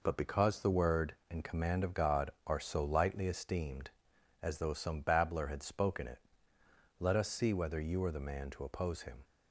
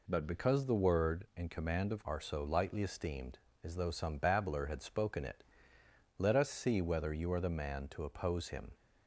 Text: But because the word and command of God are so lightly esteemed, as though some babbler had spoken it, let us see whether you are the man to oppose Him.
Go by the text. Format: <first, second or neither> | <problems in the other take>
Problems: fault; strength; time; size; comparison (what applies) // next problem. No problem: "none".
first | skips "God"; at 2.0 s